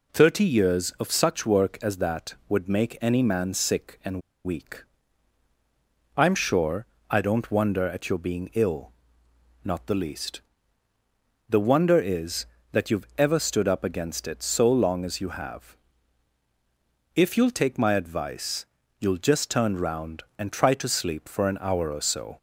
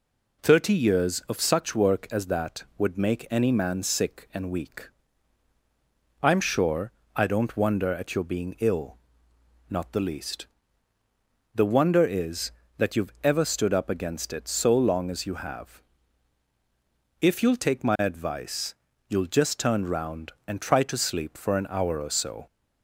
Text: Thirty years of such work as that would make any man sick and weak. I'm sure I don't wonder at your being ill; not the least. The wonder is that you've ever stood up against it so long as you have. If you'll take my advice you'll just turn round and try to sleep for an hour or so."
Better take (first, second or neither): second